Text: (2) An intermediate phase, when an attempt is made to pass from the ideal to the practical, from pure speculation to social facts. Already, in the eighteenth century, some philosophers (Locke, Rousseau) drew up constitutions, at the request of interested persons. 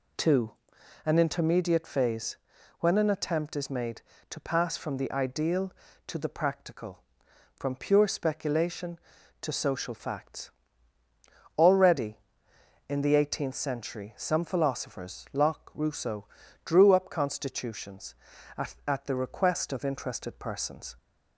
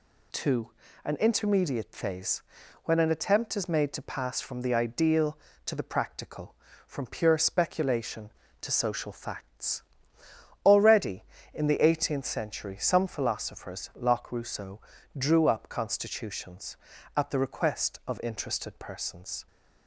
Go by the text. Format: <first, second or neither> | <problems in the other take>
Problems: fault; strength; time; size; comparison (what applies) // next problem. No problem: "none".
second | says "at" twice; at 18.8 s